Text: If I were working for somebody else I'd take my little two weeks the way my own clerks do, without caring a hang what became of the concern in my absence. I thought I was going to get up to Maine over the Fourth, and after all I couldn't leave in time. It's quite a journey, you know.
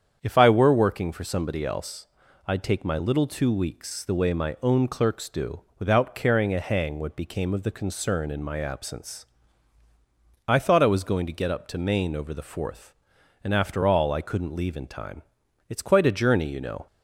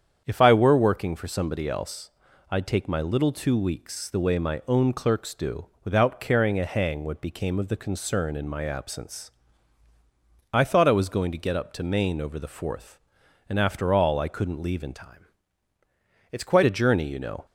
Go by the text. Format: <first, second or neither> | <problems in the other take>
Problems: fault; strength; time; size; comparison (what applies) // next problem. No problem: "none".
first | starts louder than the rest; strong; until 1.2 s; 8 dB; strong in the first // pauses between "else" and "I'd"; at 2.0 s; 0.40 s long; also in the first // changes voice from "time" to "quite"; from 14.9 to 16.6 s; 1.7 s long